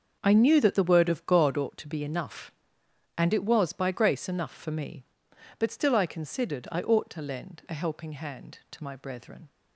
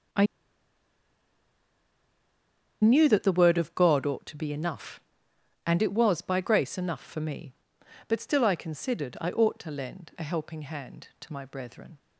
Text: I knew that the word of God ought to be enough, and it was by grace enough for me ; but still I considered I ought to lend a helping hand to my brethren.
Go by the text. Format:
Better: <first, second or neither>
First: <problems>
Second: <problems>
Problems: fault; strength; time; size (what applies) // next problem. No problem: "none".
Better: first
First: starts louder than the rest; until 1.2 s; 6.5 dB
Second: starts louder than the rest; until 3.7 s; 6.5 dB // pauses between "I" and "knew"; strong; at 0.2 s; 2.5 s long